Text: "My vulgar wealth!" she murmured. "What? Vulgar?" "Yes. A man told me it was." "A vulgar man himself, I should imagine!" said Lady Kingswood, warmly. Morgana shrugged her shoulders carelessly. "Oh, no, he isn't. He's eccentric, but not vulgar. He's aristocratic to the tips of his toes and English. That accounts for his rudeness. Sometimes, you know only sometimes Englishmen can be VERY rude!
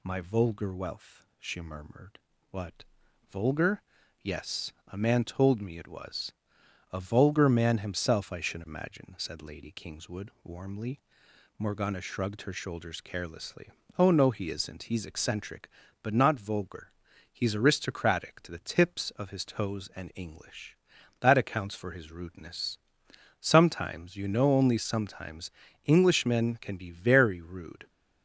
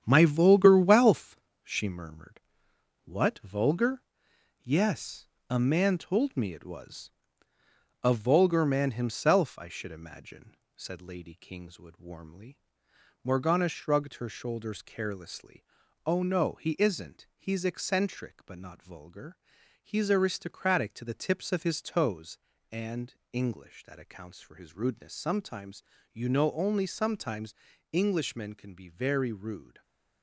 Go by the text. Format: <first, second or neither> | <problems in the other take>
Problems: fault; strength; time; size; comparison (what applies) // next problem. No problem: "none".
first | gets quieter; throughout; 6.5 dB // pauses between "and" and "English"; slight; at 23.1 s; 0.18 s long // pauses between "sometimes" and "Englishmen"; at 27.5 s; 0.38 s long; also in the first